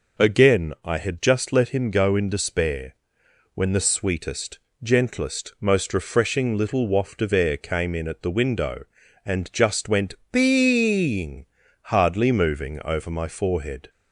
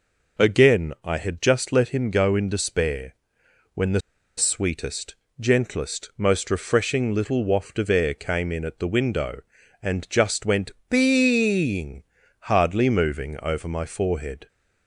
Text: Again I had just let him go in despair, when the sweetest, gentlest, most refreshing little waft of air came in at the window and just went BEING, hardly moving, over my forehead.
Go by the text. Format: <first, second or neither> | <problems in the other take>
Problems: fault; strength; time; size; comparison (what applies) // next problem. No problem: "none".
first | pauses between "the" and "sweetest"; at 4.0 s; 0.36 s long // pauses between "went" and "BEING"; slight; at 10.7 s; 0.18 s long; slight in the first